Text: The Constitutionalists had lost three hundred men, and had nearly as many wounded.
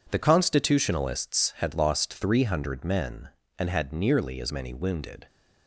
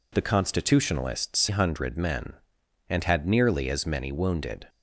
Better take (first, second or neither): first